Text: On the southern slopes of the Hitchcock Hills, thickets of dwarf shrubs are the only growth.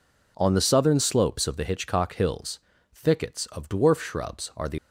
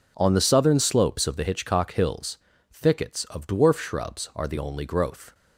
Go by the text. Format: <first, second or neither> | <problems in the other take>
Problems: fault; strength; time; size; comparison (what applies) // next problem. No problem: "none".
second | stops before "only growth"; at 4.7 s